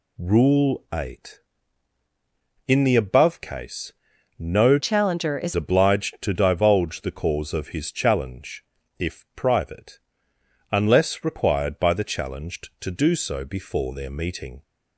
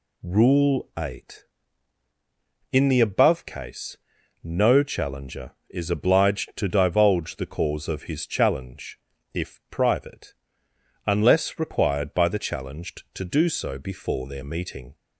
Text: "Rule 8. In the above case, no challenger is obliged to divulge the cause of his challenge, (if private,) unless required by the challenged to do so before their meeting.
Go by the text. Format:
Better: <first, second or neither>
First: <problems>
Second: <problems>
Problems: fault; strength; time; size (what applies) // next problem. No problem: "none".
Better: second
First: changes voice from "challenger" to "is"; from 4.7 to 5.5 s; 0.8 s long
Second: none